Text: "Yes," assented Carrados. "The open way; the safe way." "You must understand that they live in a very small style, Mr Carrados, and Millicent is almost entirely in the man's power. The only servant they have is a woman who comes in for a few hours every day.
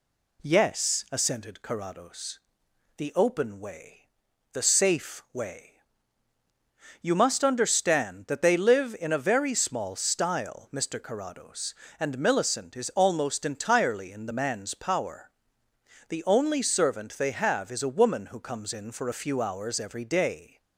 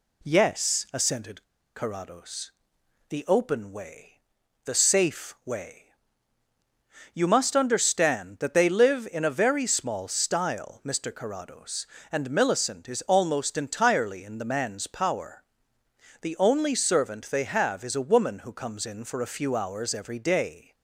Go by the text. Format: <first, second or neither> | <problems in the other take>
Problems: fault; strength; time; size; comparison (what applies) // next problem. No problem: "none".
first | pauses between "assented" and "Carrados"; slight; at 1.4 s; 0.33 s long